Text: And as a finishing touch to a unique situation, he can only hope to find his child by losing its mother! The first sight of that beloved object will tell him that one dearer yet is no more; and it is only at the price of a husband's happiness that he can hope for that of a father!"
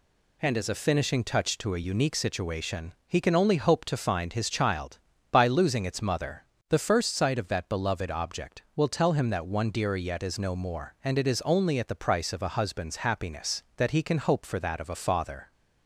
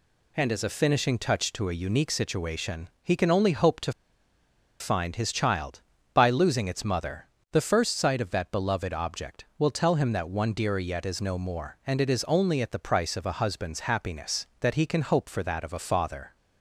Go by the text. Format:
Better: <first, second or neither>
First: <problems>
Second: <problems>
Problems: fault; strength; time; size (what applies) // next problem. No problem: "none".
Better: first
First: none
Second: pauses between "to" and "find"; noticeable; at 3.9 s; 0.88 s long